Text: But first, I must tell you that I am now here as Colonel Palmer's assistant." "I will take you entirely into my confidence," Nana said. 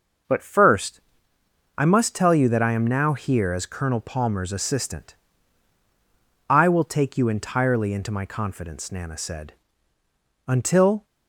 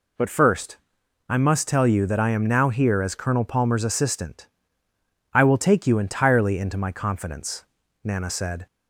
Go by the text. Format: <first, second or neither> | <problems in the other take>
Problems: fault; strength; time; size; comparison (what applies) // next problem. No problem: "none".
second | goes on to say "Until"; from 10.4 s on; 0.56 s long